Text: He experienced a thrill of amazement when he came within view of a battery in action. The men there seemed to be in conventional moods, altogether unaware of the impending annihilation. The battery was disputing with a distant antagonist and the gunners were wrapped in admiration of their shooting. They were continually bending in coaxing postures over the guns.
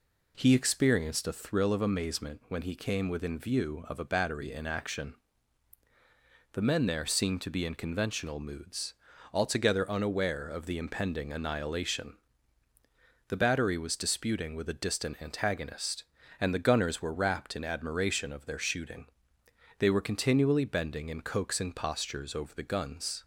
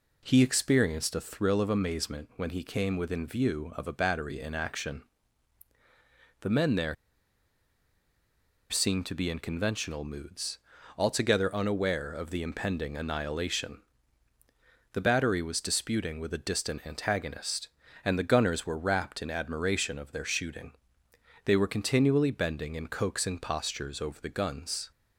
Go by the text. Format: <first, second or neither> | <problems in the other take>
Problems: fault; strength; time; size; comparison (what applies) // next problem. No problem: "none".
first | pauses between "there" and "seemed"; strong; at 6.9 s; 1.7 s long